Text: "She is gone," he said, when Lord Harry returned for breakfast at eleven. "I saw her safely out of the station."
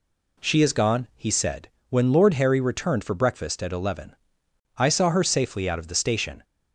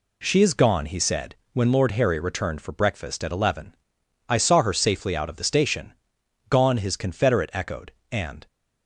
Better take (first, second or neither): first